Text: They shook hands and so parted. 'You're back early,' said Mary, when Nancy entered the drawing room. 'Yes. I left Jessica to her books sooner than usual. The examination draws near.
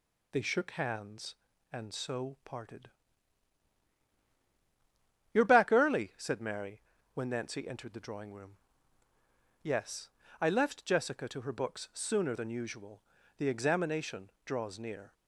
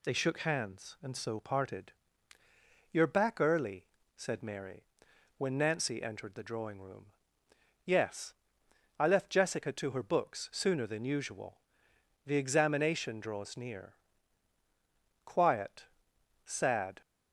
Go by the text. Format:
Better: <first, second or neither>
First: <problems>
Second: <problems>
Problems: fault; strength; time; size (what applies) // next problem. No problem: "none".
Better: first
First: none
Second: goes on to say "Quiet sad"; strong; from 15.2 s on; 1.7 s long